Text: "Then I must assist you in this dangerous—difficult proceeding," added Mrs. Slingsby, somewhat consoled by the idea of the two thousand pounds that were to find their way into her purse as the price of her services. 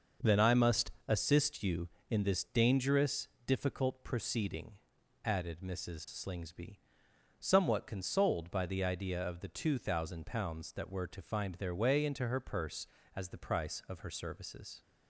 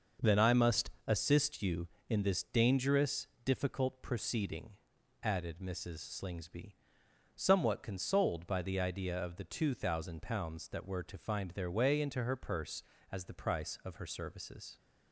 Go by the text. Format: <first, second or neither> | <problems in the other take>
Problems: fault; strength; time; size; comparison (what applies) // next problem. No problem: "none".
neither | starts louder than the rest; noticeable; the same in both // pauses between "must" and "assist"; slight; the same in both